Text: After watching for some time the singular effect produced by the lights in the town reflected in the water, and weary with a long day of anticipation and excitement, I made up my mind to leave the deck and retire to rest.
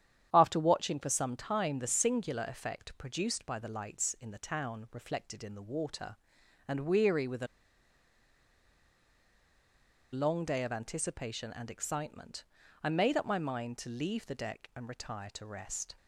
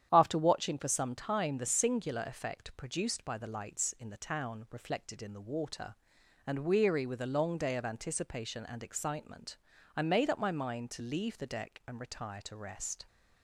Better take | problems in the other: second | starts louder than the rest; strong; until 1.3 s; 9.5 dB; strong in the second // pauses between "a" and "long"; strong; at 7.4 s; 2.6 s long

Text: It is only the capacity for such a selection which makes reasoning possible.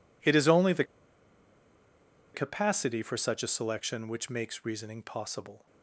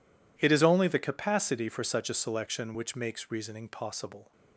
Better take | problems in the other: second | pauses between "the" and "capacity"; strong; at 0.8 s; 1.5 s long

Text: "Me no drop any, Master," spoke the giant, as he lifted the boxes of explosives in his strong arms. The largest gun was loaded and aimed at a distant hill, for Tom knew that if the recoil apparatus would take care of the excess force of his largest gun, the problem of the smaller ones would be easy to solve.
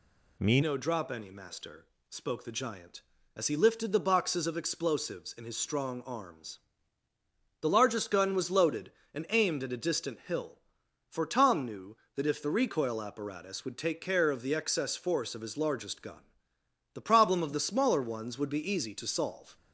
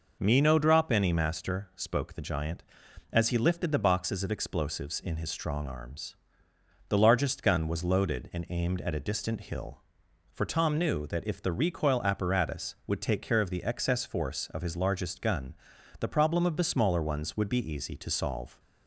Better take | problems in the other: second | changes voice at "no"; from 0.6 s on; 18.9 s long

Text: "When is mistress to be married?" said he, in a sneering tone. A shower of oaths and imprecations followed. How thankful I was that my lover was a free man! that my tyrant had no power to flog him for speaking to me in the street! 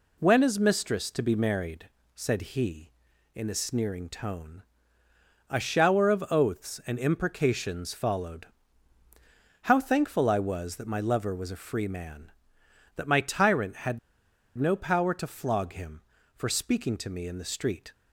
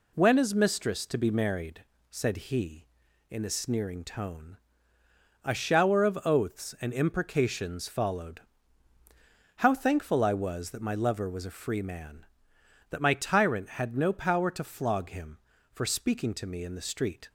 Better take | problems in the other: second | pauses between "had" and "no"; noticeable; at 13.9 s; 0.59 s long

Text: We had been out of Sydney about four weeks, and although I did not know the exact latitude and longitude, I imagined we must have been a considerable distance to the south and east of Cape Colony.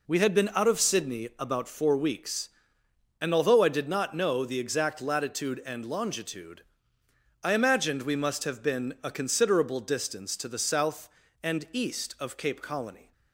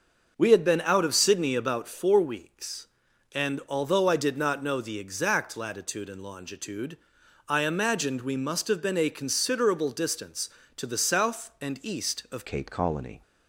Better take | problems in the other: first | starts louder than the rest; until 1.3 s; 6 dB // changes voice at "Cape"; from 12.4 s on; 0.8 s long

